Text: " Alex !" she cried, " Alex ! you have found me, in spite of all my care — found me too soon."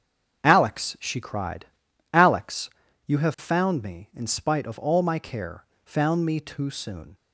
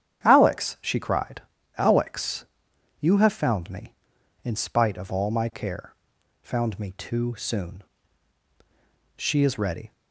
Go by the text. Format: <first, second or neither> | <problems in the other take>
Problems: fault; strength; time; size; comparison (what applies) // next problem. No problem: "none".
first | starts louder than the rest; strong; until 1.2 s; 9.5 dB; strong in the first // goes on to say "She is ready"; noticeable; from 9.1 s on; 0.74 s long